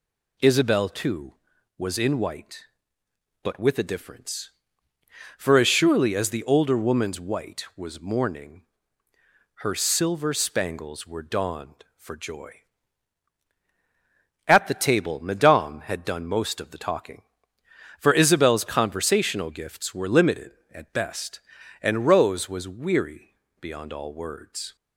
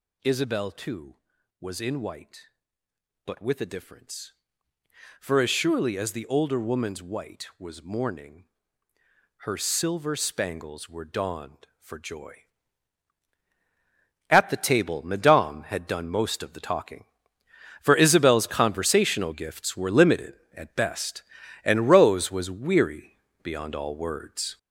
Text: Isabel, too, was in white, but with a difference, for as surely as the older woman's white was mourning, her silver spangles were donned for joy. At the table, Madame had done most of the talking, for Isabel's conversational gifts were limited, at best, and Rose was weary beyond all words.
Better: first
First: pauses between "weary" and "beyond"; slight; at 23.3 s; 0.26 s long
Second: gets louder; strong; throughout; 7.5 dB // pauses between "weary" and "beyond"; slight; at 23.1 s; 0.26 s long

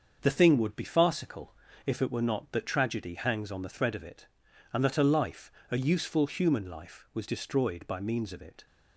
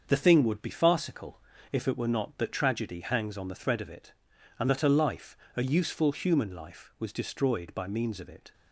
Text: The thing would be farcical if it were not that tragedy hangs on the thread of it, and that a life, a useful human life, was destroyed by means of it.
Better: neither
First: starts louder than the rest; until 1.2 s; 6.5 dB // pauses between "farcical" and "if"; slight; at 1.5 s; 0.30 s long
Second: starts louder than the rest; until 1.0 s; 6.5 dB // pauses between "farcical" and "if"; slight; at 1.4 s; 0.30 s long

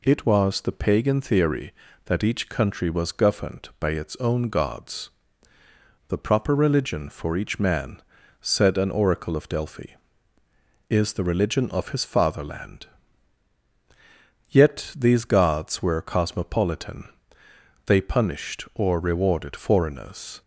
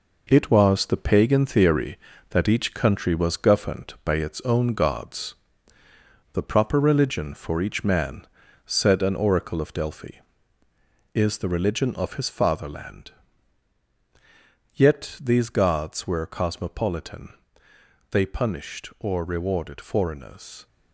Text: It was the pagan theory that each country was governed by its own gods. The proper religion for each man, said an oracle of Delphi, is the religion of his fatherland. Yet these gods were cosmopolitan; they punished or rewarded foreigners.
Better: first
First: none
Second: gets quieter; strong; throughout; 7.5 dB

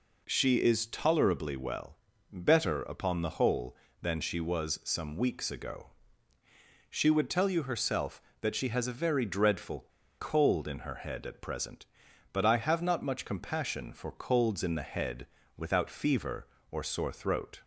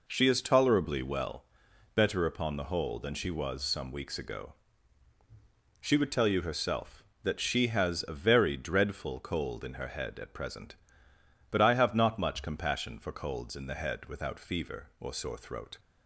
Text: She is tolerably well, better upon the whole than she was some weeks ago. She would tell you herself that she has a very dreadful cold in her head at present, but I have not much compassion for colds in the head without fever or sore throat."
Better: second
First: pauses between "dreadful" and "cold"; slight; at 9.8 s; 0.32 s long // pauses between "head" and "without"; slight; at 15.2 s; 0.30 s long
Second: none

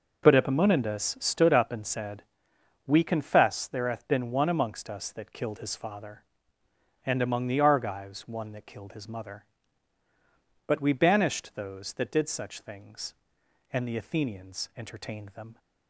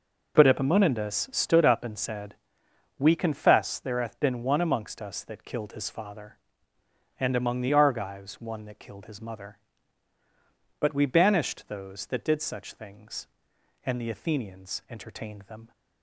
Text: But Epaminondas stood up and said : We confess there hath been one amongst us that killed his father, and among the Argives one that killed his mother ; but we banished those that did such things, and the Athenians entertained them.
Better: neither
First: none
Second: none

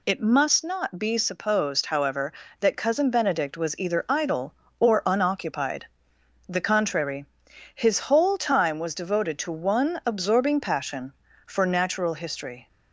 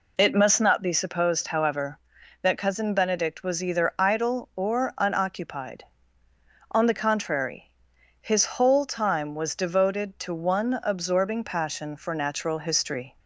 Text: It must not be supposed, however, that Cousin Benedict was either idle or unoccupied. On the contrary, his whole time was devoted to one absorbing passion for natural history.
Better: second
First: skips "On"; at 6.1 s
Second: none

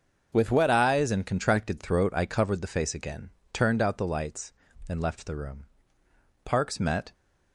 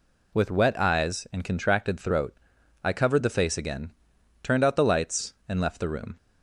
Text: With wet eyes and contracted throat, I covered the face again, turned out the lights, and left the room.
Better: second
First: starts louder than the rest; until 1.3 s; 6.5 dB // goes on to say "Parks met"; noticeable; from 6.4 s on; 0.70 s long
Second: none

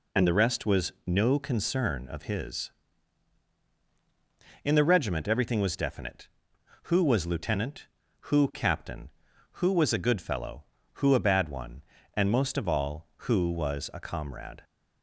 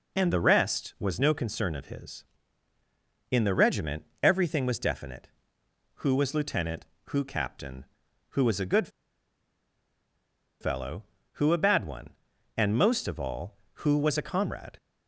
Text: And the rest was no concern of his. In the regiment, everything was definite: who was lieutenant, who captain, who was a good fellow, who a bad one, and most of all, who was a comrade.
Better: first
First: none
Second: pauses between "good" and "fellow"; strong; at 8.8 s; 1.7 s long

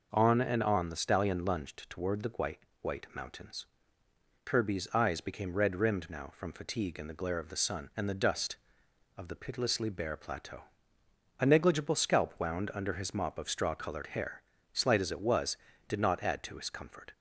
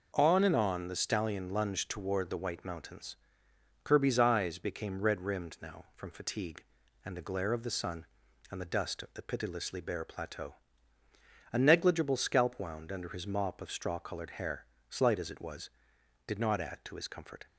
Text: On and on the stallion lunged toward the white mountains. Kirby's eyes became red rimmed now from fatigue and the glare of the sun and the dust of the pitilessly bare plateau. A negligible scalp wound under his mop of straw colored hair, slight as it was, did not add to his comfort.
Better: second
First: says "white" twice; at 2.8 s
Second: none

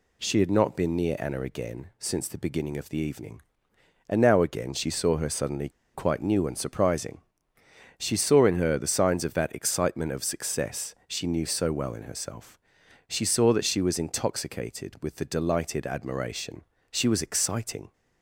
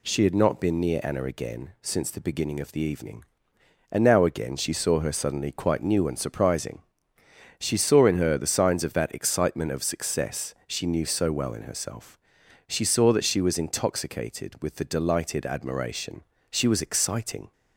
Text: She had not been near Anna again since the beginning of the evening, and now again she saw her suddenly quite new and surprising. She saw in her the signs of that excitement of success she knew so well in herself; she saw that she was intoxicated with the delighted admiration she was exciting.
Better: second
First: pauses between "suddenly" and "quite"; slight; at 5.7 s; 0.23 s long // pauses between "admiration" and "she"; slight; at 16.6 s; 0.26 s long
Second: pauses between "admiration" and "she"; slight; at 16.2 s; 0.26 s long

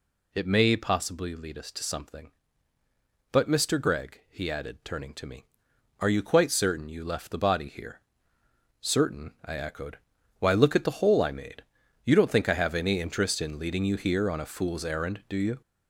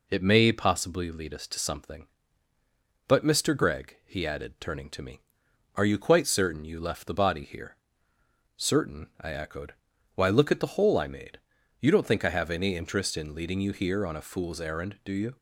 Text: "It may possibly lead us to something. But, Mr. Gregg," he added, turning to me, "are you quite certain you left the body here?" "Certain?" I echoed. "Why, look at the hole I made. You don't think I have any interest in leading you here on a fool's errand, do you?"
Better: second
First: gets louder; throughout; 6.5 dB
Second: none

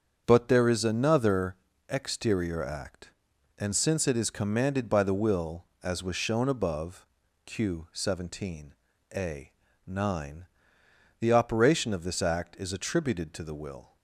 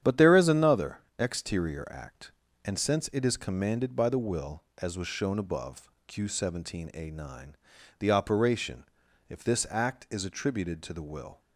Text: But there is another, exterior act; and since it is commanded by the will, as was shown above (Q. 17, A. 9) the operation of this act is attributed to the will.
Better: first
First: starts louder than the rest; strong; until 1.2 s; 7.5 dB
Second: starts louder than the rest; strong; until 1.2 s; 9 dB // says "if" for "of"; at 9.2 s

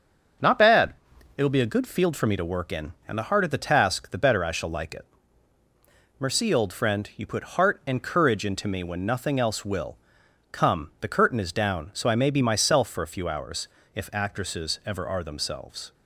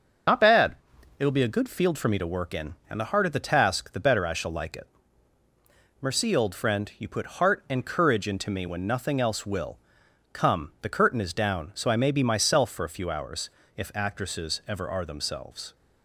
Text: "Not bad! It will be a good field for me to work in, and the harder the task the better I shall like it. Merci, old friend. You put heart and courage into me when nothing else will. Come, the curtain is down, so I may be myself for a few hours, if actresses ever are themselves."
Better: first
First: starts louder than the rest; until 1.8 s; 6.5 dB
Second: loses the start of "Not"; at 0.2 s; 50 ms // starts louder than the rest; until 1.7 s; 6.5 dB

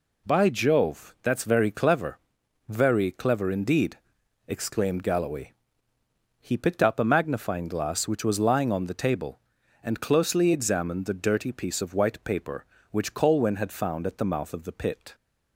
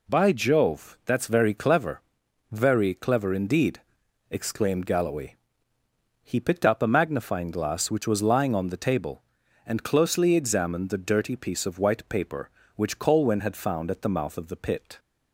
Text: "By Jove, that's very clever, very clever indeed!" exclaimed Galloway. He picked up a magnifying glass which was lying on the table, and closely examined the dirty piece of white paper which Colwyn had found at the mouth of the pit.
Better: neither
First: none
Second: none

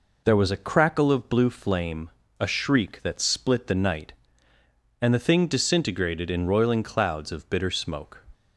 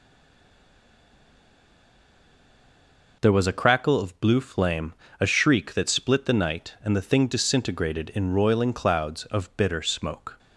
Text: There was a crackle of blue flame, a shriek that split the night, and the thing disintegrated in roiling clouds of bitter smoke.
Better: first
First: none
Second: stays silent before the first word; strong; until 3.2 s; 3.2 s long

